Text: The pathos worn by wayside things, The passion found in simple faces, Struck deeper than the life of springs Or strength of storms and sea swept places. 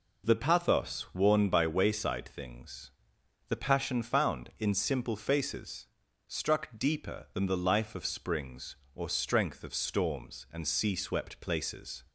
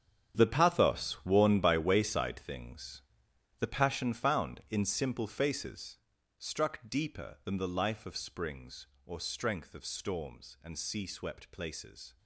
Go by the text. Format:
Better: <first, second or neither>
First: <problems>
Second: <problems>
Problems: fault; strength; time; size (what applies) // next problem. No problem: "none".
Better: first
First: none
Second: gets quieter; strong; throughout; 14 dB